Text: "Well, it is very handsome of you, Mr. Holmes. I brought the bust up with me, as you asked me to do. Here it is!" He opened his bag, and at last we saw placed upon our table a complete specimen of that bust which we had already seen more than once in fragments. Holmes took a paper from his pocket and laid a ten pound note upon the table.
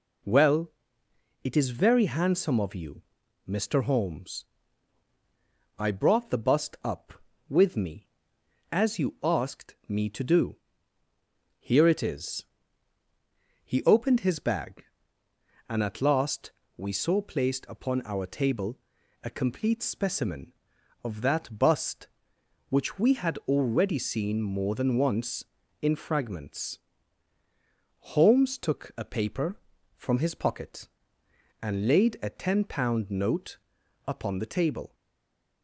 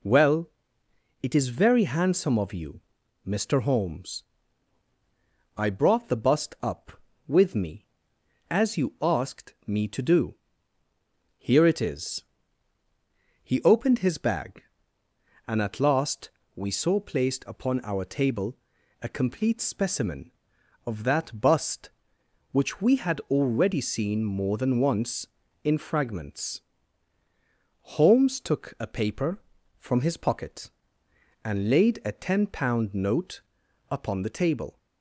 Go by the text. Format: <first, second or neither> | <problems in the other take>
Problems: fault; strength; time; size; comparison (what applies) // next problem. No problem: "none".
second | pauses between "last" and "we"; slight; at 16.5 s; 0.26 s long; slight in the second // pauses between "table" and "a"; noticeable; at 18.7 s; 0.46 s long; noticeable in the second // pauses between "note" and "upon"; noticeable; at 33.5 s; 0.48 s long; noticeable in the second // stays silent after the last word; slight; from 34.9 s on; 0.7 s long